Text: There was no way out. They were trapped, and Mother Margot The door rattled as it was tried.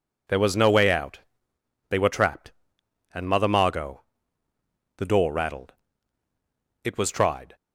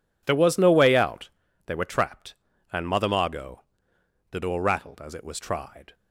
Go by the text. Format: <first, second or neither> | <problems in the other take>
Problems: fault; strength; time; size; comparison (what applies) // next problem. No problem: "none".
second | pauses between "Margot" and "The"; noticeable; at 4.0 s; 0.94 s long; noticeable in the second // skips "as"; at 6.2 s